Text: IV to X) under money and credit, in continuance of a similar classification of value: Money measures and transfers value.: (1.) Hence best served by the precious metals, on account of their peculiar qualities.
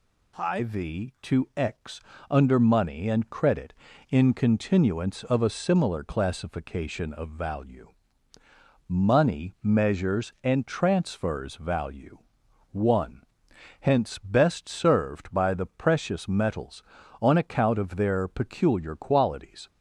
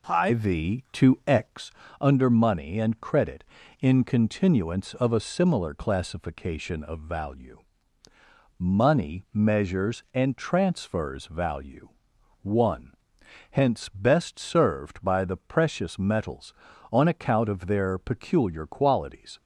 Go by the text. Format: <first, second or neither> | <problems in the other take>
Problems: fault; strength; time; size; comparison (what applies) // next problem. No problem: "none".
first | starts louder than the rest; until 1.6 s; 3.5 dB